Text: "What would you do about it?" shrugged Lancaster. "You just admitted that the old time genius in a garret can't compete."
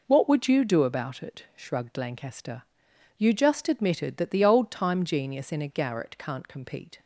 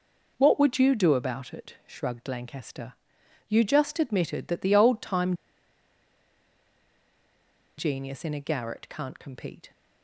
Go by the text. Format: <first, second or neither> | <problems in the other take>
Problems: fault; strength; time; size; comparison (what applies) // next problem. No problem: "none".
first | pauses between "time" and "genius"; strong; at 5.3 s; 2.4 s long